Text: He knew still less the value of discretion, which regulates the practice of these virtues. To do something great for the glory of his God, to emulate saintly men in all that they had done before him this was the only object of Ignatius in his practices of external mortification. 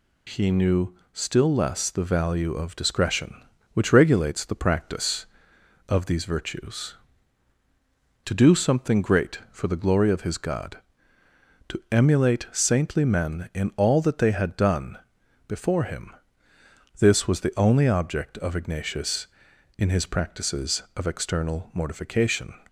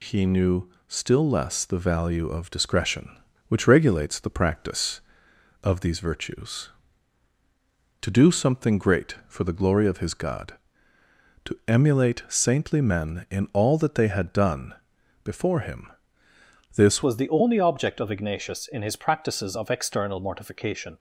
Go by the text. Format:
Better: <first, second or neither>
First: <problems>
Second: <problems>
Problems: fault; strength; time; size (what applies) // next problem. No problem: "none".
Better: first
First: pauses between "knew" and "still"; slight; at 0.9 s; 0.20 s long // pauses between "done" and "before"; noticeable; at 14.9 s; 0.48 s long // pauses between "him" and "this"; noticeable; at 16.1 s; 0.86 s long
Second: pauses between "knew" and "still"; slight; at 0.6 s; 0.20 s long // pauses between "done" and "before"; noticeable; at 14.7 s; 0.48 s long // pauses between "him" and "this"; noticeable; at 15.8 s; 0.86 s long // changes voice at "was"; from 17.0 s on; 3.9 s long